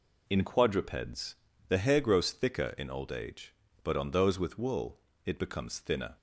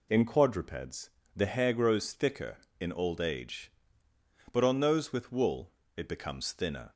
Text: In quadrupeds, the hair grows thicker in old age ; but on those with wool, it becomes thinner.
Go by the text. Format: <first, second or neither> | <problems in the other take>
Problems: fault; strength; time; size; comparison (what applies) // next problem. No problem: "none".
neither | none